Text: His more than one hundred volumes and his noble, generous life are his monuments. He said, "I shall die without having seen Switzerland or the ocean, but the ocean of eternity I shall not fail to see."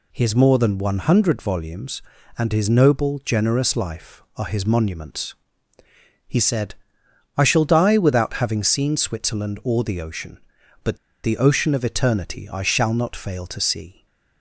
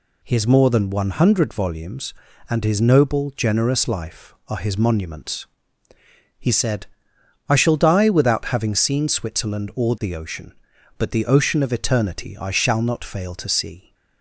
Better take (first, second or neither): second